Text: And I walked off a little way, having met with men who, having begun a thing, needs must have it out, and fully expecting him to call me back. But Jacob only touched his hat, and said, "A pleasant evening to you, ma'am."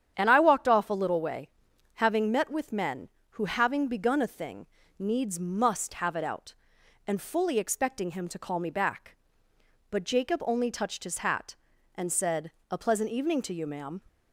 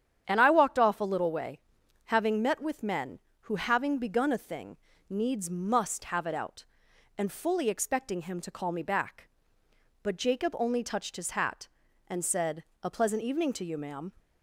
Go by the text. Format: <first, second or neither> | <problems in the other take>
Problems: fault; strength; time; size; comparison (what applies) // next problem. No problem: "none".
neither | starts louder than the rest; strong; the same in both